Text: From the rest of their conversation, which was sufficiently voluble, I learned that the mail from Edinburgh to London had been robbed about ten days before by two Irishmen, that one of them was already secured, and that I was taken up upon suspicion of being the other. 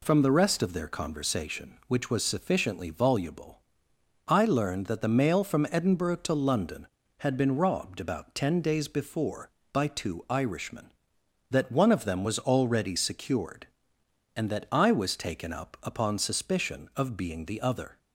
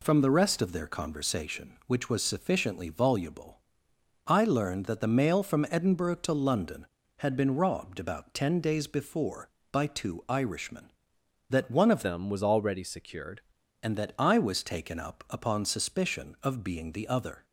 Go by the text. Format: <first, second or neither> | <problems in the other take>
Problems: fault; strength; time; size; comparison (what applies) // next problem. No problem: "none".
first | changes voice from "them" to "secured"; from 12.0 to 13.4 s; 1.4 s long